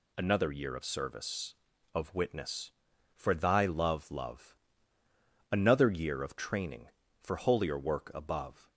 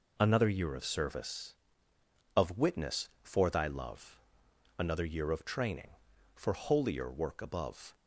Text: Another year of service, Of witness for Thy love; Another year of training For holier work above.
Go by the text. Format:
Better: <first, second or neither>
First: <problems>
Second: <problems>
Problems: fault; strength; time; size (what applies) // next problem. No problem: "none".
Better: second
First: says "love" twice; at 4.1 s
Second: none